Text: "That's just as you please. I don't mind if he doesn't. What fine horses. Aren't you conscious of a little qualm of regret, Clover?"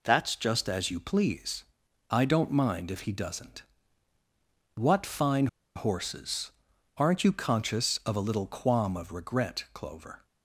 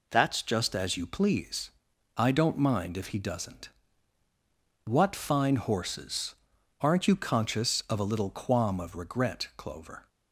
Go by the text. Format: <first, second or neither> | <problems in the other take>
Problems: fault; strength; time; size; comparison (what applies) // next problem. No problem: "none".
second | pauses between "fine" and "horses"; slight; at 5.4 s; 0.29 s long